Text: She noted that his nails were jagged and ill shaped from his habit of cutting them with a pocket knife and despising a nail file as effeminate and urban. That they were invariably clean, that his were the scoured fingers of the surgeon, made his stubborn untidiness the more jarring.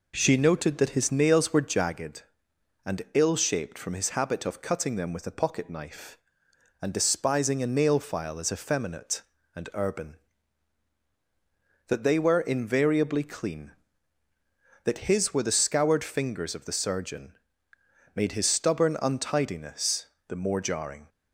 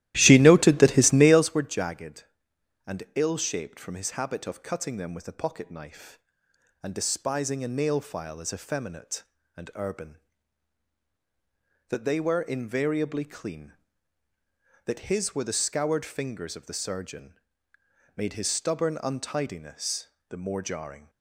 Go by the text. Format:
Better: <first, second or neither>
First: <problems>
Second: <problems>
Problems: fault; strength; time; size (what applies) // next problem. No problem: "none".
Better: first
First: pauses between "untidiness" and "the"; slight; at 20.0 s; 0.22 s long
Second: starts louder than the rest; strong; until 1.5 s; 14.5 dB // pauses between "untidiness" and "the"; slight; at 20.0 s; 0.22 s long